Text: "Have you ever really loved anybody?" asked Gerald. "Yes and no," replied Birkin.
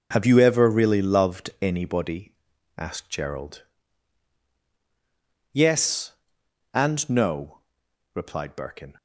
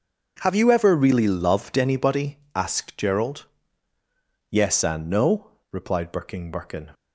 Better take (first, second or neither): first